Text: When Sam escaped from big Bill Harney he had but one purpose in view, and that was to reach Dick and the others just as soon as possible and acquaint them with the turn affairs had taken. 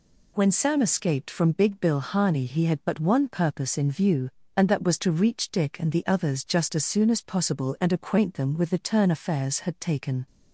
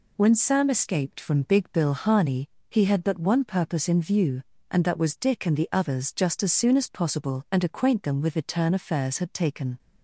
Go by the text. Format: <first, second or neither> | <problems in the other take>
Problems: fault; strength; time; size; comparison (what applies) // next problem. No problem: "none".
first | pauses between "Harney" and "he"; slight; at 2.4 s; 0.22 s long // skips "to reach"; at 5.1 s